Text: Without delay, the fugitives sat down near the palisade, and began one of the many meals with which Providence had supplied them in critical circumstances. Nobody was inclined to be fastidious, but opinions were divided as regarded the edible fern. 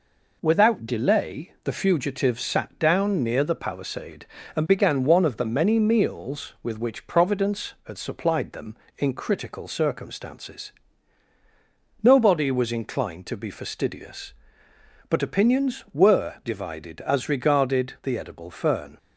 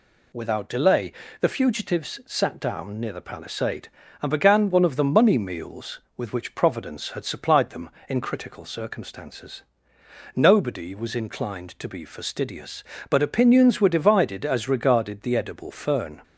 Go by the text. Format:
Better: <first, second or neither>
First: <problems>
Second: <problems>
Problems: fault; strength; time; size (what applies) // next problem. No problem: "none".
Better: first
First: none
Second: says "money" for "many"; at 5.0 s